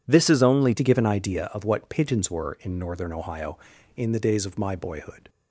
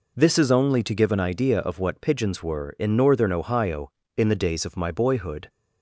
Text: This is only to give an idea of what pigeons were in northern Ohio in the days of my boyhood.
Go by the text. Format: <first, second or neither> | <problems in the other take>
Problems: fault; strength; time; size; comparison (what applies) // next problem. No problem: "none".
second | changes voice at "to"; from 0.7 s on; 4.5 s long